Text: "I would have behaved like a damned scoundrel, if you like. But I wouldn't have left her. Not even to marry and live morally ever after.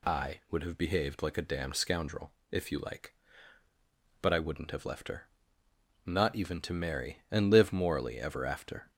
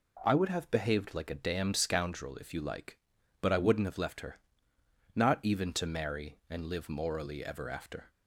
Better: neither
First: none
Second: none

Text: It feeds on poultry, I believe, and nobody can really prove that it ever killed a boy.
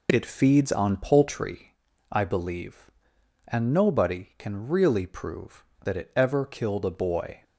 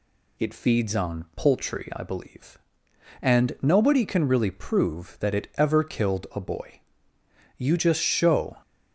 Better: first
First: none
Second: goes on to say "You just show"; noticeable; from 7.5 s on; 1.0 s long

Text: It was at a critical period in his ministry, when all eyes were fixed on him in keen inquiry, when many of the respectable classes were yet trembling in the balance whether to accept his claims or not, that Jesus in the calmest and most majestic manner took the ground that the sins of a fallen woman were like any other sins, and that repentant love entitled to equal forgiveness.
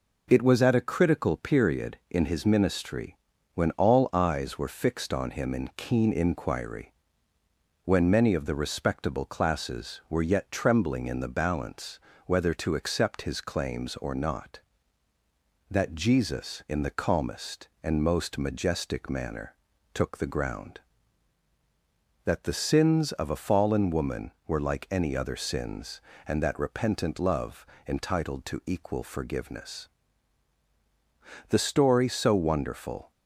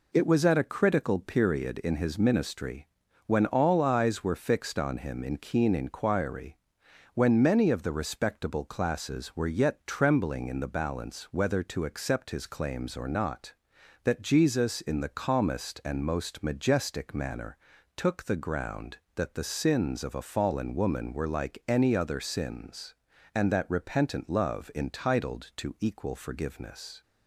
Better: second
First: pauses between "balance" and "whether"; slight; at 11.9 s; 0.28 s long // pauses between "manner" and "took"; at 19.5 s; 0.40 s long // pauses between "love" and "entitled"; slight; at 27.6 s; 0.22 s long // goes on to say "The story so wonderful"; from 31.4 s on; 1.6 s long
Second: pauses between "manner" and "took"; at 17.5 s; 0.40 s long

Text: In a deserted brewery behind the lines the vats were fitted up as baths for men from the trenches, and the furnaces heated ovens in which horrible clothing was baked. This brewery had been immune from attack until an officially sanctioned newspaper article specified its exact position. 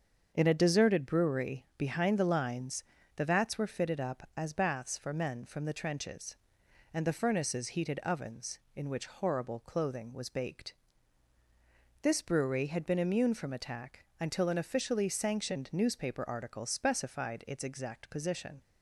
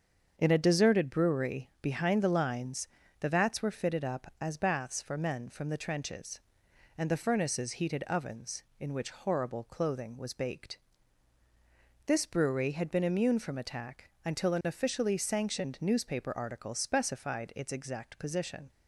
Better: neither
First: starts louder than the rest; until 1.3 s; 7 dB // pauses between "lines" and "the"; slight; at 2.8 s; 0.34 s long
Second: starts louder than the rest; until 1.3 s; 7 dB // pauses between "lines" and "the"; slight; at 2.8 s; 0.34 s long

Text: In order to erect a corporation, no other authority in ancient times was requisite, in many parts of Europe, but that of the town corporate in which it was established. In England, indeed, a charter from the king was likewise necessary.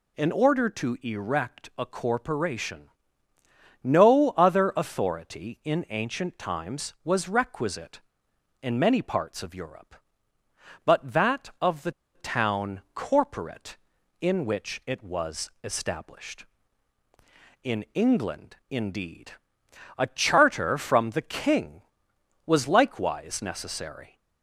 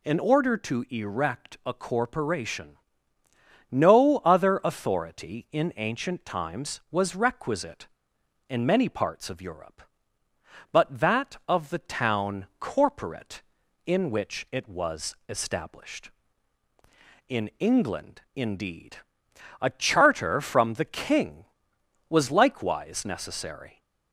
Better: second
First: pauses between "the" and "town"; slight; at 11.9 s; 0.24 s long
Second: none

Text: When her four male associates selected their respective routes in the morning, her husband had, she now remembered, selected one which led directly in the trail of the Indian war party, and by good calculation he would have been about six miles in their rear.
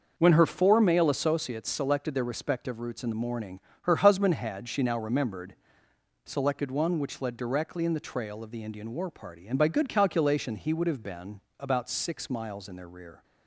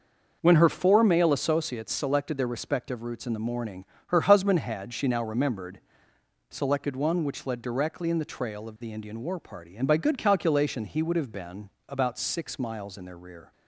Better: neither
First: pauses between "been" and "about"; slight; at 11.4 s; 0.18 s long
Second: pauses between "been" and "about"; slight; at 11.6 s; 0.18 s long

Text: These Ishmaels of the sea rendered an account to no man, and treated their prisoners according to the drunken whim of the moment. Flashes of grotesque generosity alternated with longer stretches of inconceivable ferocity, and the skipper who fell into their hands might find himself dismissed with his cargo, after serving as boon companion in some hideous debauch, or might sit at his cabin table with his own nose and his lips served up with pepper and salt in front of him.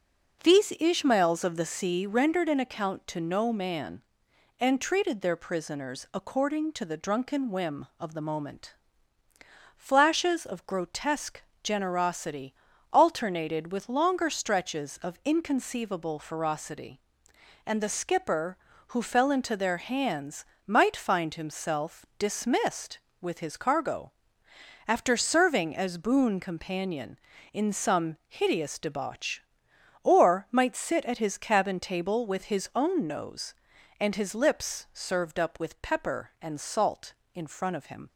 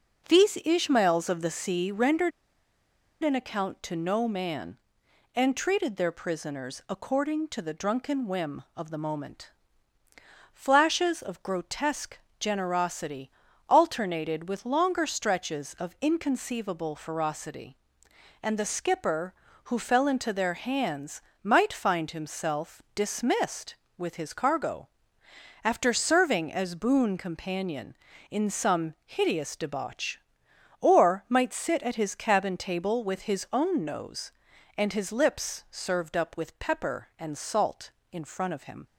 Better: first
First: pauses between "grotesque" and "generosity"; slight; at 11.4 s; 0.24 s long // pauses between "generosity" and "alternated"; at 12.5 s; 0.40 s long // pauses between "hands" and "might"; slight; at 20.4 s; 0.24 s long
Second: pauses between "rendered" and "an"; noticeable; at 2.3 s; 0.92 s long // pauses between "grotesque" and "generosity"; slight; at 12.1 s; 0.24 s long // pauses between "generosity" and "alternated"; at 13.2 s; 0.40 s long // pauses between "hands" and "might"; slight; at 21.2 s; 0.24 s long

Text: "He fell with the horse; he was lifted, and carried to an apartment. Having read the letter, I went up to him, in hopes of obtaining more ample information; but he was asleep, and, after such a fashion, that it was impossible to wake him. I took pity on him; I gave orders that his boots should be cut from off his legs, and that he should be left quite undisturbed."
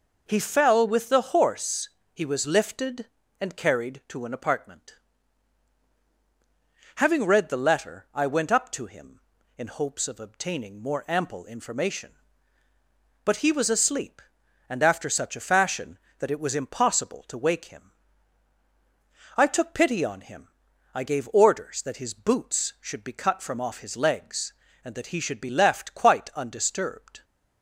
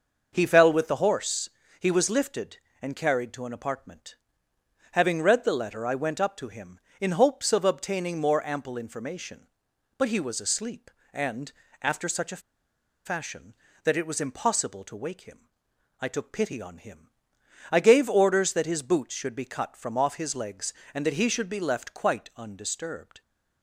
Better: first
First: none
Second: starts louder than the rest; noticeable; until 1.3 s; 6 dB // pauses between "a" and "fashion"; noticeable; at 12.4 s; 0.63 s long

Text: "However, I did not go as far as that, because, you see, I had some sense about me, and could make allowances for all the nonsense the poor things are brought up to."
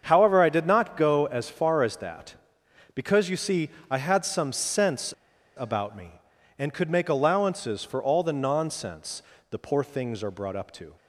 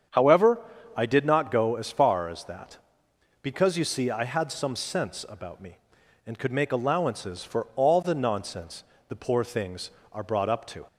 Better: second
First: starts louder than the rest; strong; until 1.0 s; 7 dB // pauses between "sense" and "about"; at 5.1 s; 0.43 s long // pauses between "nonsense" and "the"; slight; at 9.2 s; 0.26 s long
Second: starts louder than the rest; strong; until 1.4 s; 8 dB // pauses between "nonsense" and "the"; slight; at 8.8 s; 0.24 s long

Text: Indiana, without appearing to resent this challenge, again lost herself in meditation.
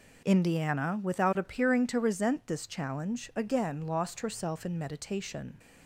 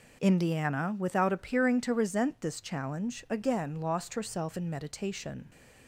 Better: neither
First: none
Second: none

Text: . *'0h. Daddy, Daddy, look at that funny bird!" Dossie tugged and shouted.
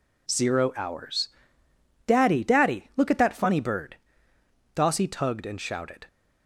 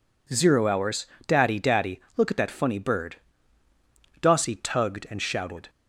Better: neither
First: none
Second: none

